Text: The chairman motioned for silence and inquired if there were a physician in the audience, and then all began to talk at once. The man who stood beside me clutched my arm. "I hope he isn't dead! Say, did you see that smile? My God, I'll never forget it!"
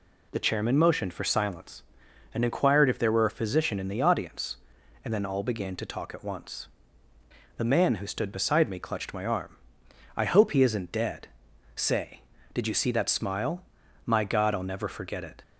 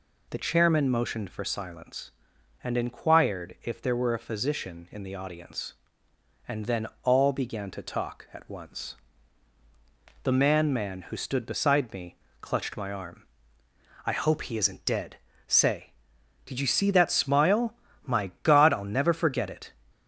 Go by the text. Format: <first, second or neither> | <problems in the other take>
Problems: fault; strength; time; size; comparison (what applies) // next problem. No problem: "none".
first | pauses between "then" and "all"; slight; at 6.8 s; 0.18 s long // says "man" twice; at 10.7 s // pauses between "me" and "clutched"; slight; at 12.1 s; 0.24 s long